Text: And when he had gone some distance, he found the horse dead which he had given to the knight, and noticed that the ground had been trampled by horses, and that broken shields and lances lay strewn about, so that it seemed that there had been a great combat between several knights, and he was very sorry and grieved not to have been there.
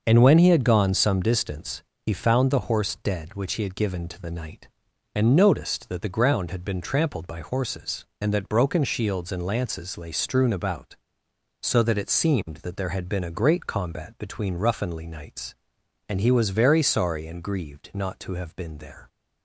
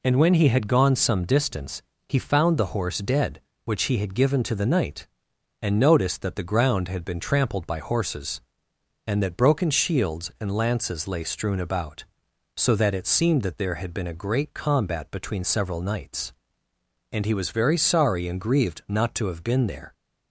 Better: second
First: starts louder than the rest; until 1.0 s; 6 dB // says "ruffinly" for "several"; at 14.5 s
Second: none

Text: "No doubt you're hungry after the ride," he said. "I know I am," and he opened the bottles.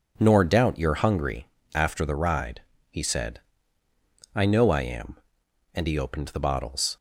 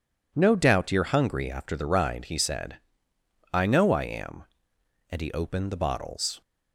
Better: second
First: says "Nor" for "No"; at 0.1 s // pauses between "hungry" and "after"; slight; at 1.4 s; 0.28 s long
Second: none

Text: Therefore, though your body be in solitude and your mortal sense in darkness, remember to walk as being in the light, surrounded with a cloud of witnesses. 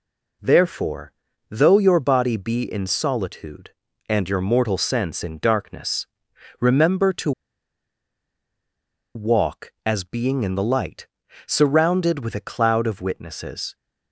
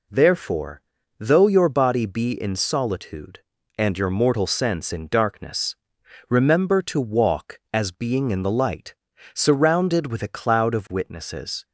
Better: second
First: pauses between "to" and "walk"; strong; at 7.3 s; 1.8 s long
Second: none

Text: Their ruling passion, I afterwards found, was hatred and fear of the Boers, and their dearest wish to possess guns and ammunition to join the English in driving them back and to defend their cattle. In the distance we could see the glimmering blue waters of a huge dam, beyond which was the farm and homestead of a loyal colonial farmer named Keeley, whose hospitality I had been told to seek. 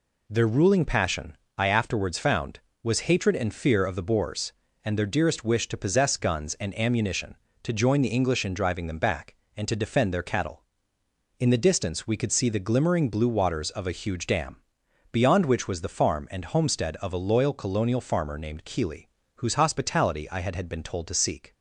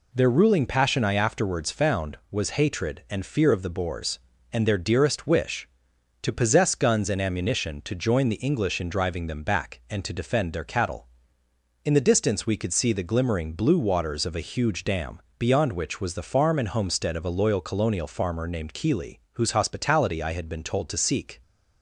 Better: second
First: says "had" twice; at 20.5 s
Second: none

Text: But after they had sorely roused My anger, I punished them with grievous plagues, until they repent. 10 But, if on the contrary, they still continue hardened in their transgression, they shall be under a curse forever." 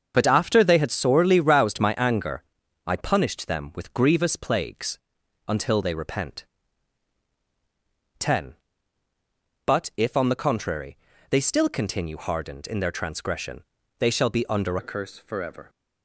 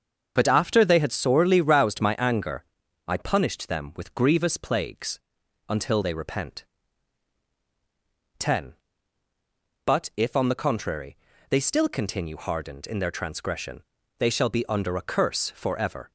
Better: second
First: starts louder than the rest; until 1.1 s; 7 dB // changes voice at "a"; from 14.7 s on; 0.9 s long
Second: starts louder than the rest; until 1.3 s; 7 dB

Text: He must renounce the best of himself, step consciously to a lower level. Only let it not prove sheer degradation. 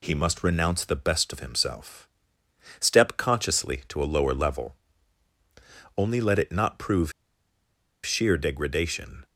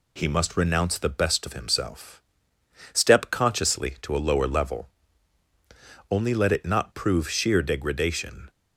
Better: second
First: pauses between "prove" and "sheer"; noticeable; at 7.1 s; 0.92 s long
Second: none

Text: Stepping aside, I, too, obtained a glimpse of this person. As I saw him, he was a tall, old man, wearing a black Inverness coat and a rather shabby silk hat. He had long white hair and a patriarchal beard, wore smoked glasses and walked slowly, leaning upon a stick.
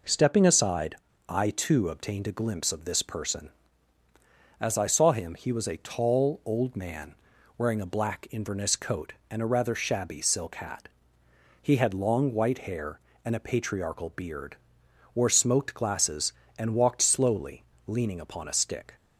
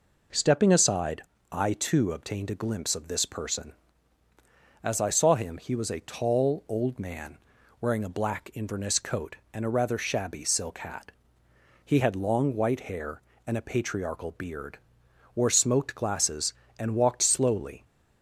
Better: first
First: none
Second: stops before "leaning upon a stick"; at 17.8 s

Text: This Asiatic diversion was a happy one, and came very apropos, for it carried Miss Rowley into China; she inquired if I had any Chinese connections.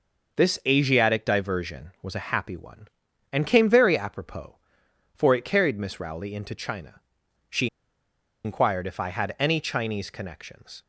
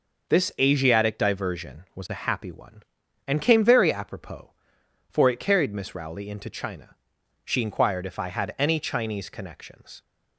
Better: second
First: pauses between "she" and "inquired"; noticeable; at 7.6 s; 0.78 s long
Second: none

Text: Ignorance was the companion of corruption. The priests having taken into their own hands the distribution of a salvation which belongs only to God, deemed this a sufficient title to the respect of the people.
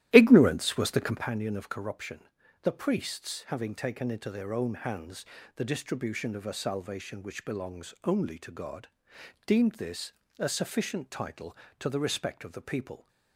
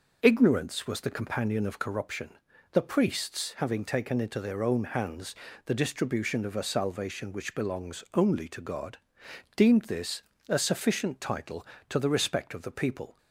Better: second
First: starts louder than the rest; strong; until 1.3 s; 13 dB // pauses between "hands" and "the"; slight; at 5.2 s; 0.32 s long // pauses between "this" and "a"; slight; at 10.1 s; 0.26 s long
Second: pauses between "hands" and "the"; slight; at 5.3 s; 0.32 s long // pauses between "this" and "a"; slight; at 10.2 s; 0.26 s long

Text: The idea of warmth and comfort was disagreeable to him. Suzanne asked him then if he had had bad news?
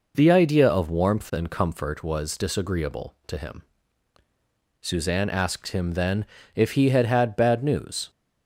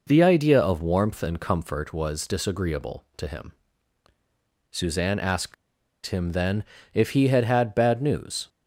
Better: first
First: pauses between "then" and "if"; slight; at 6.2 s; 0.30 s long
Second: pauses between "asked" and "him"; noticeable; at 5.5 s; 0.51 s long // pauses between "then" and "if"; slight; at 6.6 s; 0.30 s long

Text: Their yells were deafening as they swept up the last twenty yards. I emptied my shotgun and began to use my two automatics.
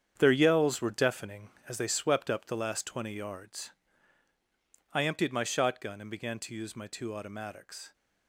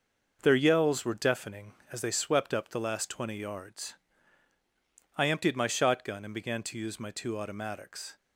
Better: second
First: gets quieter; strong; throughout; 10 dB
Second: none

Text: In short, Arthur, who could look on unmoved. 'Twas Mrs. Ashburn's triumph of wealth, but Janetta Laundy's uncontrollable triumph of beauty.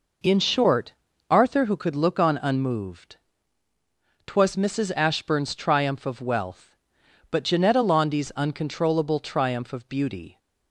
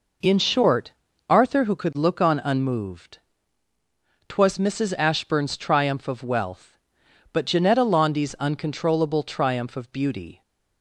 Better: neither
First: none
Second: none

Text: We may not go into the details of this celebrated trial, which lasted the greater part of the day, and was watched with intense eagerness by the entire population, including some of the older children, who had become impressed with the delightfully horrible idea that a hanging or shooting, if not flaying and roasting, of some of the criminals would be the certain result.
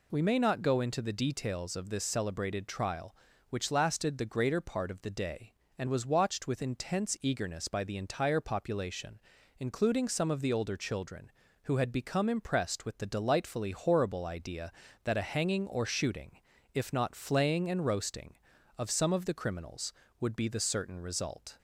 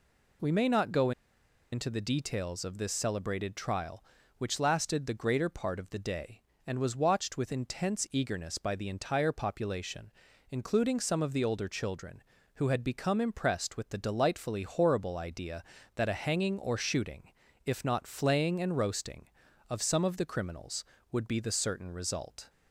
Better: first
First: none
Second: pauses between "go" and "into"; noticeable; at 1.1 s; 0.61 s long

